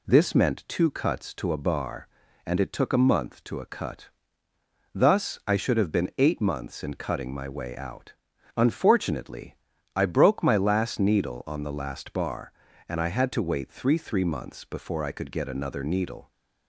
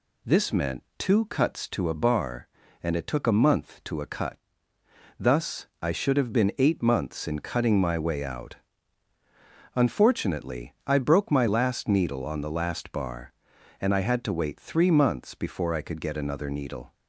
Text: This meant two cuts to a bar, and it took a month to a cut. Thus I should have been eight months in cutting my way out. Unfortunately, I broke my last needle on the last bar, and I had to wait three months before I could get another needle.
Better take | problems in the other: second | says "three" twice; at 13.9 s

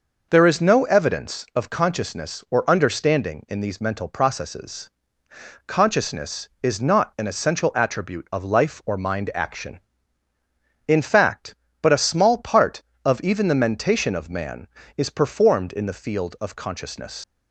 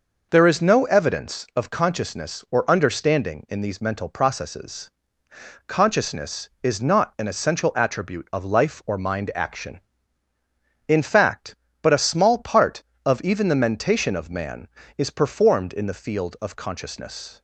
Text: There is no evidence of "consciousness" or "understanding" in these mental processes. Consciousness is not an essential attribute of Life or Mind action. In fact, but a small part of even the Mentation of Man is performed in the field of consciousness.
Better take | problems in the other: second | leaves "consciousness" unfinished; at 17.2 s; 165 ms

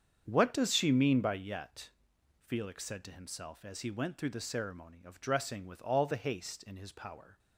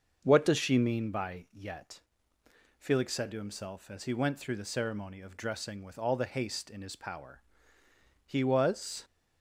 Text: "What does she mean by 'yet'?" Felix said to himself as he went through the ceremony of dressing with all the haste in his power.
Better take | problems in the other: first | starts louder than the rest; until 1.2 s; 6.5 dB; strong in the first // goes on to say "He was"; noticeable; from 8.2 s on; 0.78 s long

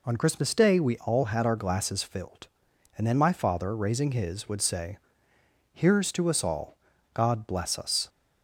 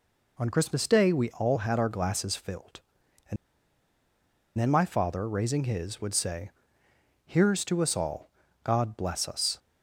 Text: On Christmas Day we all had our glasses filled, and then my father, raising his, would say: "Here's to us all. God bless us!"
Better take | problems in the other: first | pauses between "and" and "then"; at 3.3 s; 1.2 s long

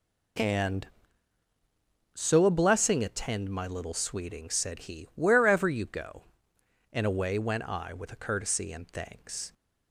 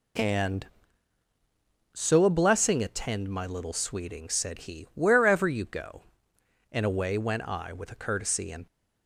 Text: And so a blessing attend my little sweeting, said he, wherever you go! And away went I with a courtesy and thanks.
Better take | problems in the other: first | stops before "thanks"; at 8.6 s

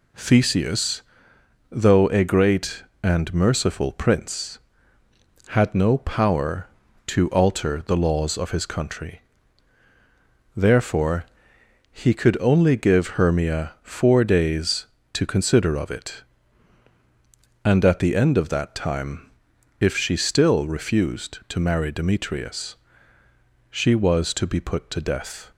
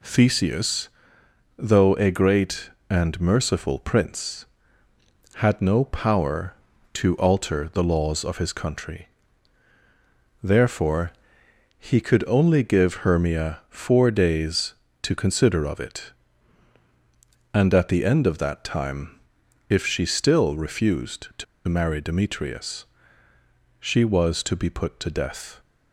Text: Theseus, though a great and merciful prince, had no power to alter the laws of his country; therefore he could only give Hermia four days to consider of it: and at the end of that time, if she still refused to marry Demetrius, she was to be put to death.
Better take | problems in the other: first | pauses between "therefore" and "he"; noticeable; at 11.1 s; 0.66 s long; noticeable in the first // pauses between "to" and "marry"; slight; at 21.4 s; 0.23 s long

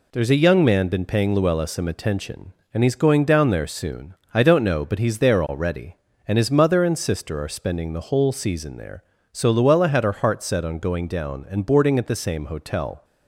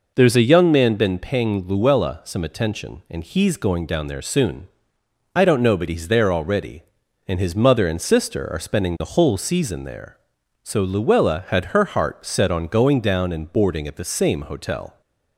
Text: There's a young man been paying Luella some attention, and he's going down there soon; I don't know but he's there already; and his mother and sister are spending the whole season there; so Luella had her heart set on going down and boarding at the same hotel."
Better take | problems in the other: neither | none

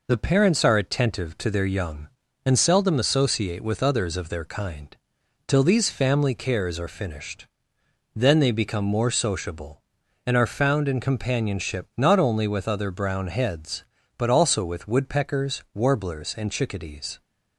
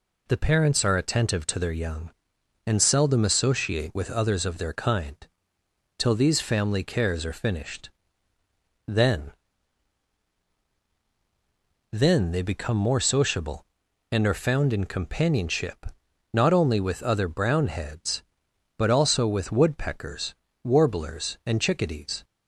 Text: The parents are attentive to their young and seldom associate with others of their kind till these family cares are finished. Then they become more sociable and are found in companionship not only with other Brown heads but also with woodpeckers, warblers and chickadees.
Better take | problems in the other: first | pauses between "kind" and "till"; noticeable; at 5.1 s; 0.82 s long; noticeable in the first // says "Then" twice; at 11.9 s // pauses between "companionship" and "not"; noticeable; at 15.8 s; 0.46 s long

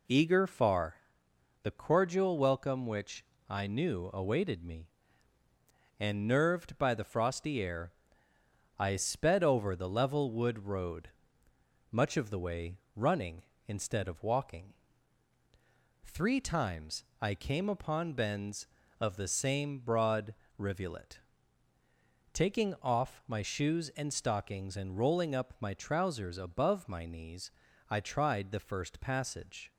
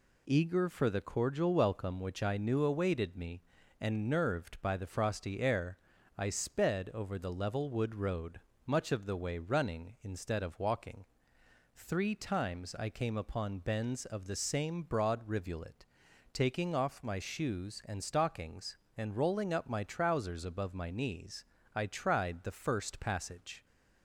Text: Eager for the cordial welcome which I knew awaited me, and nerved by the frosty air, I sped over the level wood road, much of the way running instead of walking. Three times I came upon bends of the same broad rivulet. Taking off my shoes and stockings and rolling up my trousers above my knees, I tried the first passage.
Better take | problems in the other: second | says "far" for "for"; at 0.4 s // pauses between "which" and "I"; slight; at 3.2 s; 0.24 s long // pauses between "way" and "running"; slight; at 12.7 s; 0.18 s long // pauses between "times" and "I"; slight; at 17.0 s; 0.16 s long // pauses between "broad" and "rivulet"; slight; at 20.3 s; 0.24 s long

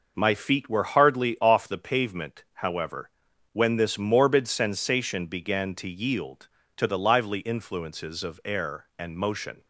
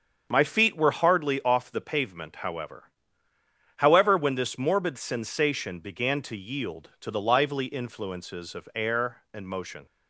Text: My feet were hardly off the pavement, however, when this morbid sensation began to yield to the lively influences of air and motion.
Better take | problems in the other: first | starts louder than the rest; strong; until 1.3 s; 7 dB // says "however" twice; at 3.7 s

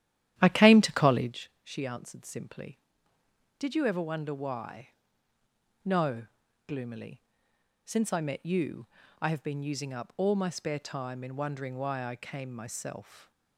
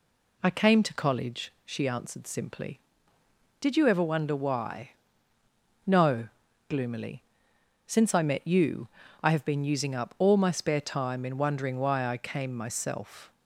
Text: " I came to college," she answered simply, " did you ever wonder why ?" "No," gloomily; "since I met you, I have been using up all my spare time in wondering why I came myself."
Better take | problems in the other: second | starts louder than the rest; strong; until 1.4 s; 12 dB

